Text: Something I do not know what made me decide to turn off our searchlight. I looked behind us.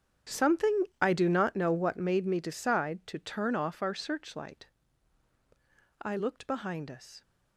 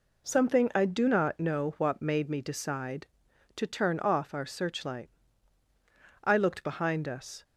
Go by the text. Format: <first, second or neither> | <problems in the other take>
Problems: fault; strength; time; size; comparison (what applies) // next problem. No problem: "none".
second | gets quieter; strong; throughout; 17 dB // pauses between "Something" and "I"; slight; at 0.8 s; 0.16 s long